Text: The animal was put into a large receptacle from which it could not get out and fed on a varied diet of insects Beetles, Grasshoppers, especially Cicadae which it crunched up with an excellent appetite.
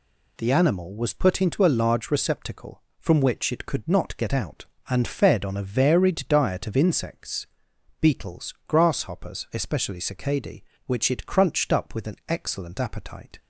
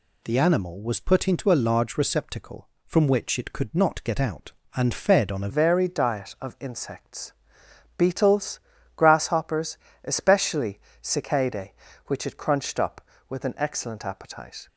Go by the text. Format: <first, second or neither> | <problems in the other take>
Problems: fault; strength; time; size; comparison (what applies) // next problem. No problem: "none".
first | changes voice at "varied"; from 5.4 s on; 9.2 s long // pauses between "insects" and "Beetles"; noticeable; at 7.3 s; 0.66 s long; noticeable in the first // pauses between "especially" and "Cicadae"; slight; at 10.7 s; 0.24 s long